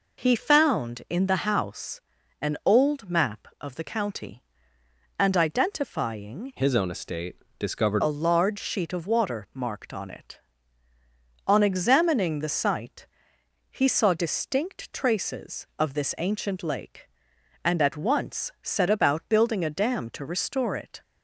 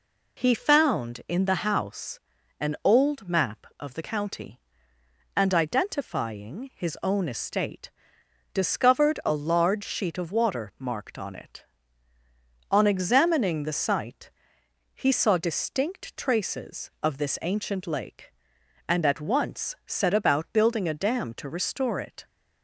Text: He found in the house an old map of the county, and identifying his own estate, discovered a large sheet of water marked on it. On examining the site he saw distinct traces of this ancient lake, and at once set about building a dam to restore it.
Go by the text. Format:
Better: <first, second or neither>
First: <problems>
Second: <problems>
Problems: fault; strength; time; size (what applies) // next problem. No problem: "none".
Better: second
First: pauses between "house" and "an"; at 2.0 s; 0.40 s long // changes voice from "his" to "discovered"; from 6.5 to 8.0 s; 1.5 s long // pauses between "site" and "he"; noticeable; at 13.0 s; 0.64 s long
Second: pauses between "house" and "an"; at 2.1 s; 0.40 s long // pauses between "site" and "he"; noticeable; at 14.2 s; 0.64 s long